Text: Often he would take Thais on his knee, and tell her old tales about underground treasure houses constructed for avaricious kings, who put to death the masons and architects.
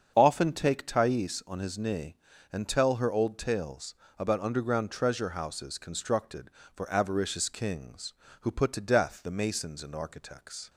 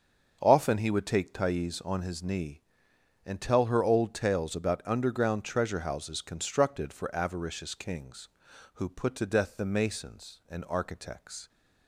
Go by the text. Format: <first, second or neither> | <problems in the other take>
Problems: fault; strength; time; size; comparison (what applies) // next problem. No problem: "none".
second | starts louder than the rest; strong; until 1.1 s; 7.5 dB; also in the second // skips "he would"; at 0.5 s // pauses between "tales" and "about"; slight; at 3.9 s; 0.20 s long